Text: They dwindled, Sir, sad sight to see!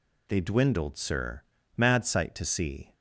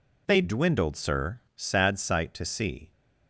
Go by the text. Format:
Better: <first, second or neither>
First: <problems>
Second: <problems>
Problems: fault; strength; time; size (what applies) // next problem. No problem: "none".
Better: second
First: says "mad" for "sad"; at 1.7 s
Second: none